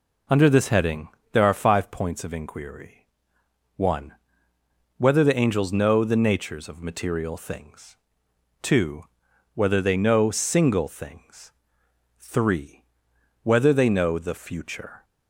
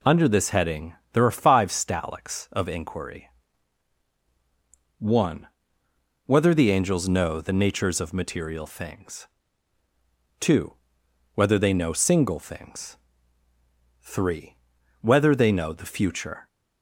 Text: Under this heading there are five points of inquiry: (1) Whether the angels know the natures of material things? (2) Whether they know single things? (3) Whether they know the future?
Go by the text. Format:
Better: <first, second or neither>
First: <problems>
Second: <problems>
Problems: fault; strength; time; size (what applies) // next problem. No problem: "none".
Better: first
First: pauses between "heading" and "there"; slight; at 1.0 s; 0.24 s long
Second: pauses between "heading" and "there"; slight; at 0.9 s; 0.18 s long // says "stalics" for "points"; at 1.7 s